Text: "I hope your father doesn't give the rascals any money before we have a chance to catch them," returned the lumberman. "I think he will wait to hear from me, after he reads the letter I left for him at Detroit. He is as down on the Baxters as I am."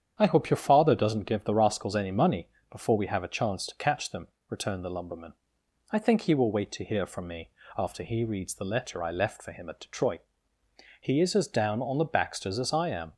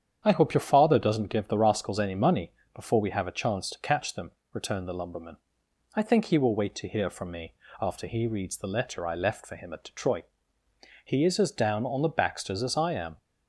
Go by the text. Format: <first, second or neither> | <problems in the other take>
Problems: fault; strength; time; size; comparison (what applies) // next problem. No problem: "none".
neither | starts louder than the rest; strong; the same in both // pauses between "money" and "before"; slight; the same in both